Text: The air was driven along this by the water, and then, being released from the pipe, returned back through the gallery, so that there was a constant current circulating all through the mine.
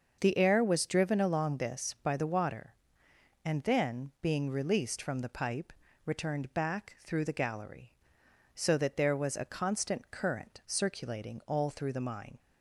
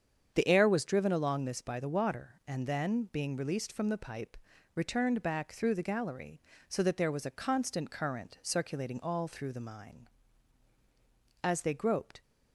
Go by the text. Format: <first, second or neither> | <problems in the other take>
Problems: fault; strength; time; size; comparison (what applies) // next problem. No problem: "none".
first | starts louder than the rest; strong; until 1.3 s; 7.5 dB; also in the first // goes on to say "As they groped"; noticeable; from 11.4 s on; 0.78 s long